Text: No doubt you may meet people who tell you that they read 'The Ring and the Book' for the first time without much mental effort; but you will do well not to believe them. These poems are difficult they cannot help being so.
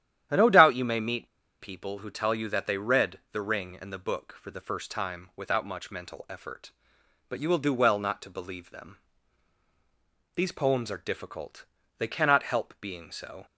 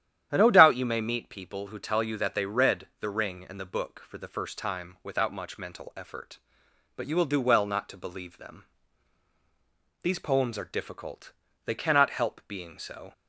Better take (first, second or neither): second